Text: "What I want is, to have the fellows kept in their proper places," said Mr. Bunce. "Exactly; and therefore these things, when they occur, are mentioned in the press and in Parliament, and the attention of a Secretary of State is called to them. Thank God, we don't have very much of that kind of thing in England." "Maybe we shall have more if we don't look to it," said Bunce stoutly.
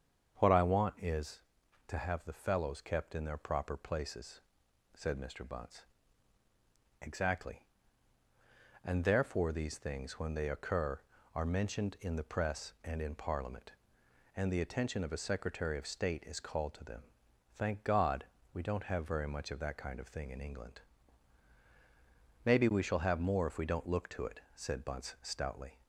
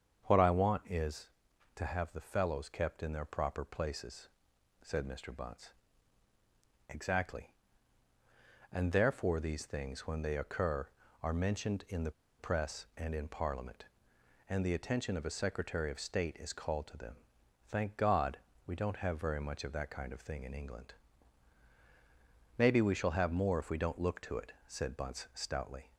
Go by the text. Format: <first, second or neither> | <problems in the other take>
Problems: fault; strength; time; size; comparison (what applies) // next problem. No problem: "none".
first | starts louder than the rest; strong; until 1.8 s; 7.5 dB; strong in the first // pauses between "the" and "press"; slight; at 12.1 s; 0.27 s long